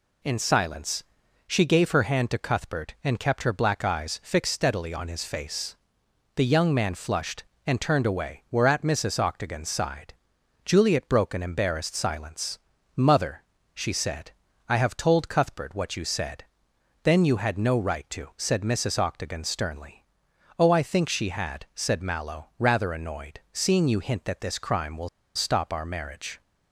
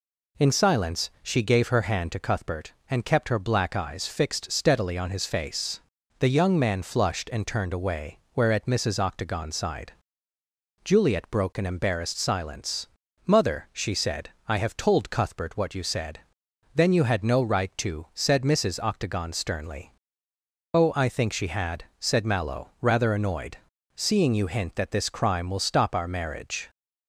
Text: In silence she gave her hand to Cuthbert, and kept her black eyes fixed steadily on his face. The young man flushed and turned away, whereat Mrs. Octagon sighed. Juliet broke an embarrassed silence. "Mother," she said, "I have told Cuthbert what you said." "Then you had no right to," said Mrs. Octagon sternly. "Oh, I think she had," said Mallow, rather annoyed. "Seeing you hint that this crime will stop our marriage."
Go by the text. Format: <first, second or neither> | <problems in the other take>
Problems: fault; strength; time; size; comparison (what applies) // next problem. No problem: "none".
second | pauses between "silence" and "she"; noticeable; at 1.0 s; 0.46 s long // pauses between "will" and "stop"; slight; at 25.0 s; 0.27 s long